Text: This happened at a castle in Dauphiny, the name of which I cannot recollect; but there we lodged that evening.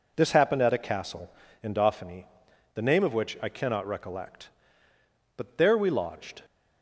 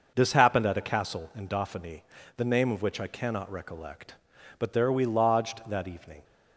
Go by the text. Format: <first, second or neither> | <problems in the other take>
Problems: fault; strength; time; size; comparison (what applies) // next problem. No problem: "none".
second | stops before "that evening"; at 6.4 s